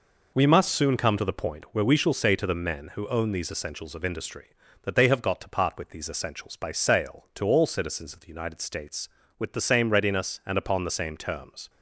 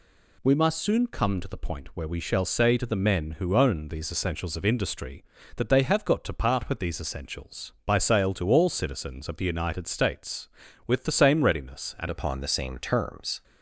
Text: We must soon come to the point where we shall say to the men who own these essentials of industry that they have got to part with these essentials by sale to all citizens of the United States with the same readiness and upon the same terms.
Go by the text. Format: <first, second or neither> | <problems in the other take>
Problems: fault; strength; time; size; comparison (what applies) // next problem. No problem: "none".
first | changes voice at "upon"; from 12.0 s on; 1.4 s long